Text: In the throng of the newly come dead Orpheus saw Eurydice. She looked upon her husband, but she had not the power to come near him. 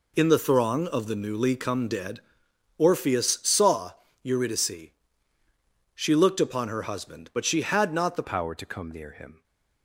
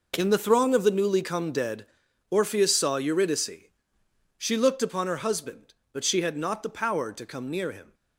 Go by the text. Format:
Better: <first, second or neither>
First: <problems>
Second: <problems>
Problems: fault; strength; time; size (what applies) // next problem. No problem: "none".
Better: second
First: pauses between "dead" and "Orpheus"; noticeable; at 2.2 s; 0.56 s long // pauses between "saw" and "Eurydice"; slight; at 3.9 s; 0.32 s long // changes voice at "power"; from 8.2 s on; 1.2 s long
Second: pauses between "dead" and "Orpheus"; at 1.8 s; 0.42 s long